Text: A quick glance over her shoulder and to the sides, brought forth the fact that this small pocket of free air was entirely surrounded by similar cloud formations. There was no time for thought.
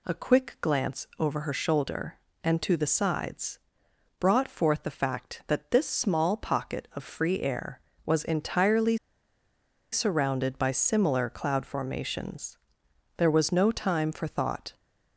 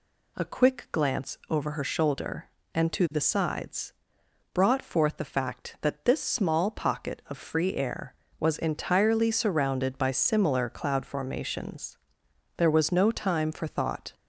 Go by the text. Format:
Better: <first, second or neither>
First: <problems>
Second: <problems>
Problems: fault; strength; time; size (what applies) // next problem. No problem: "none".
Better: second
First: pauses between "entirely" and "surrounded"; noticeable; at 8.9 s; 0.95 s long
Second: none